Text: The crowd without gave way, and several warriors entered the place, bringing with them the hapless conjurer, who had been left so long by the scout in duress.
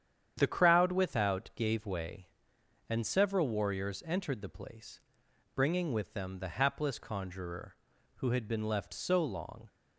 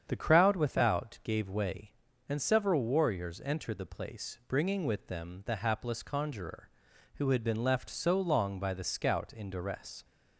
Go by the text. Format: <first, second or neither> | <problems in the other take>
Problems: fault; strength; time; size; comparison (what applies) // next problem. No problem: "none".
second | starts louder than the rest; strong; until 1.3 s; 8.5 dB; strong in the second // stops before "by the scout in duress"; at 9.6 s